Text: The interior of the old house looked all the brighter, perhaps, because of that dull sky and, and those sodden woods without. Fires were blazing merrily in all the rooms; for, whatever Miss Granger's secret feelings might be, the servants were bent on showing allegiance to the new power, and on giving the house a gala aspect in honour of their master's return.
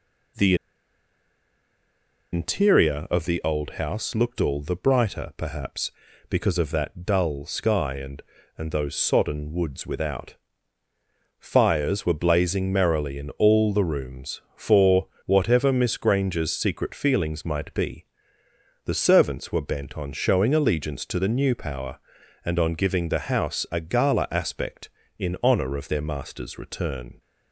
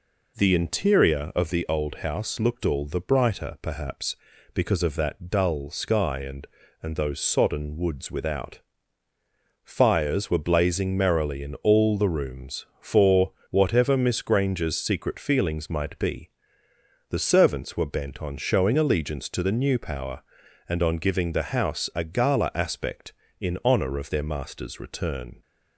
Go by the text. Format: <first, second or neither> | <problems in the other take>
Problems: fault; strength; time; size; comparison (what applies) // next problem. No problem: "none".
second | pauses between "The" and "interior"; strong; at 0.5 s; 1.7 s long